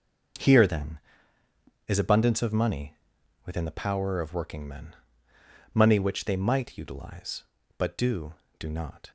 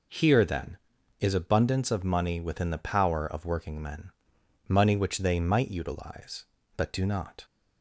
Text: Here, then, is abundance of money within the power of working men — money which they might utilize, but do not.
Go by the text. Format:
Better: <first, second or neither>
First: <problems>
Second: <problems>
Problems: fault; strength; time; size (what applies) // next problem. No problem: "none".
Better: second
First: starts louder than the rest; noticeable; until 2.2 s; 6 dB // pauses between "money" and "within"; noticeable; at 2.9 s; 0.50 s long // says "do" twice; at 8.5 s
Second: none